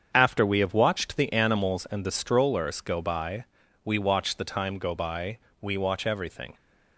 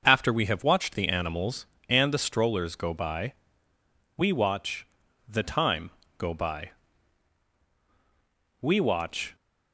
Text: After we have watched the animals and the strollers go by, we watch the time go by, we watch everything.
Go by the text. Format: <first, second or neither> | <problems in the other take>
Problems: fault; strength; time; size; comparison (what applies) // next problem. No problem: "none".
first | starts louder than the rest; noticeable; until 1.0 s; 6 dB; strong in the first // pauses between "watch" and "the"; at 4.8 s; 0.44 s long // pauses between "time" and "go"; slight; at 5.9 s; 0.26 s long // stops before "everything"; at 9.3 s